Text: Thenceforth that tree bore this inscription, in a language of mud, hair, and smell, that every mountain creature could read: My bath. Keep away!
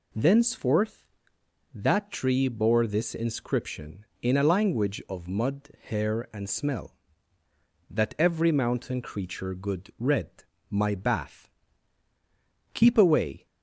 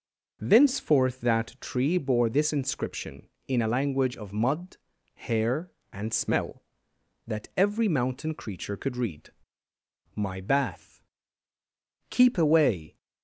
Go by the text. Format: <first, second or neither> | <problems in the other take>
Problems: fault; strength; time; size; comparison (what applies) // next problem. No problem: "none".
second | says "good" for "could"; at 9.5 s